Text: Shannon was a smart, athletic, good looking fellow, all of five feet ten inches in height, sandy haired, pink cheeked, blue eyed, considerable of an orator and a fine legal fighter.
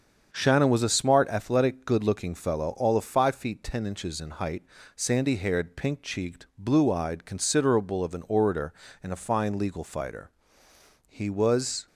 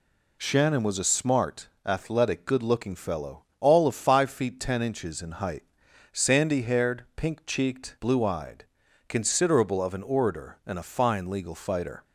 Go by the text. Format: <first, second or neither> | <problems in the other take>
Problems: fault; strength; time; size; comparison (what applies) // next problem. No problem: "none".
second | starts louder than the rest; until 1.3 s; 7 dB // goes on to say "He was"; noticeable; from 11.0 s on; 0.80 s long